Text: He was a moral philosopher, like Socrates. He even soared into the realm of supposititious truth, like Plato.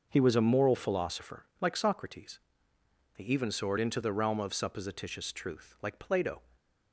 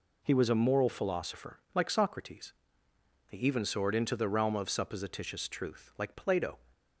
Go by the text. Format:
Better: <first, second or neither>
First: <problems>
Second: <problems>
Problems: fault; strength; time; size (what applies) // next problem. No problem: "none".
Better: second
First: starts louder than the rest; noticeable; until 1.3 s; 6 dB // stays silent after the last word; slight; from 6.4 s on; 0.5 s long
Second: none